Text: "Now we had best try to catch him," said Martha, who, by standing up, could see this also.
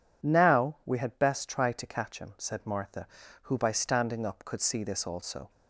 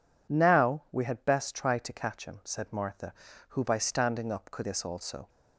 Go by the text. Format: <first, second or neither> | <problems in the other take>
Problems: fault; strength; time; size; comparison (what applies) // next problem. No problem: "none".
first | skips "see"; at 4.6 s